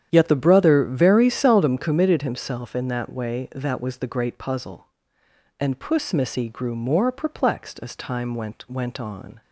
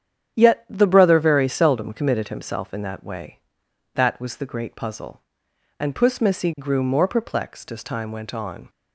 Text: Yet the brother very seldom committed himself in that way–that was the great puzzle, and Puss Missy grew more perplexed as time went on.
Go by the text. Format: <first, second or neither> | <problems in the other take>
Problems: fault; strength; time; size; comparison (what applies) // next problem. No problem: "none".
second | starts louder than the rest; strong; until 1.1 s; 9.5 dB; strong in the second // says "went" twice; at 8.7 s